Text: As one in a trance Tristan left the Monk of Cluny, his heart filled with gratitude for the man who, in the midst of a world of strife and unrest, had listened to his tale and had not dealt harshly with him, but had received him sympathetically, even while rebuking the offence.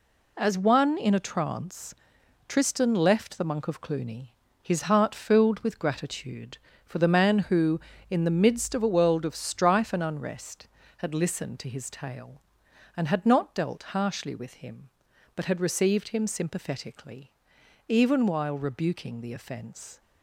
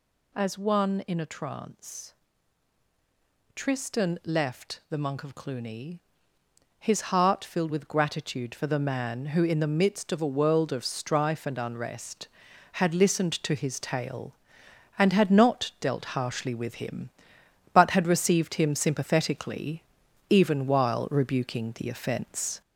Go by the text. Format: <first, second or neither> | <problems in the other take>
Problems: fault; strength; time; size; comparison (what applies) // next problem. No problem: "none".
first | gets louder; noticeable; throughout; 4 dB // pauses between "trance" and "Tristan"; strong; at 2.1 s; 1.4 s long; noticeable in the first